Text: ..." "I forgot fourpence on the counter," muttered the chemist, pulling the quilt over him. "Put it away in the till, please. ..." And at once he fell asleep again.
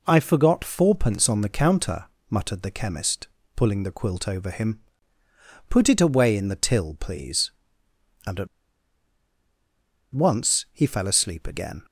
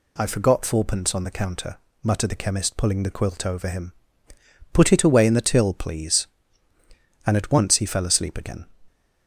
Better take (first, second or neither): second